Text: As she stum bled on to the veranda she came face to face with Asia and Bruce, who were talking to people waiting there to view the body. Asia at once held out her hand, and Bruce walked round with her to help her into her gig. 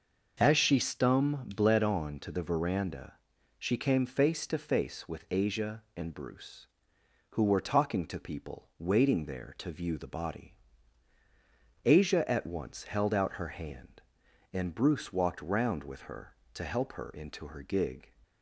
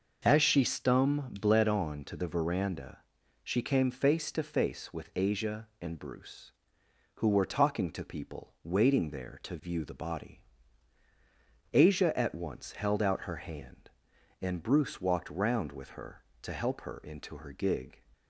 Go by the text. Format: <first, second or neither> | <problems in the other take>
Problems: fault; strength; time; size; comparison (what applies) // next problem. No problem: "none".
neither | pauses between "veranda" and "she"; the same in both